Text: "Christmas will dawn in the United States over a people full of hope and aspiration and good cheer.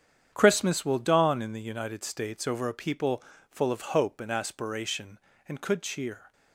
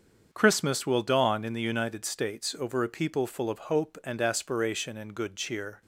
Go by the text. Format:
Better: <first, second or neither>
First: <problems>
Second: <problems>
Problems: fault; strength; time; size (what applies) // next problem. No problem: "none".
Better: second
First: starts louder than the rest; strong; until 1.3 s; 8.5 dB // pauses between "people" and "full"; slight; at 3.2 s; 0.28 s long // says "could" for "good"; at 5.5 s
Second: starts louder than the rest; strong; until 1.3 s; 7 dB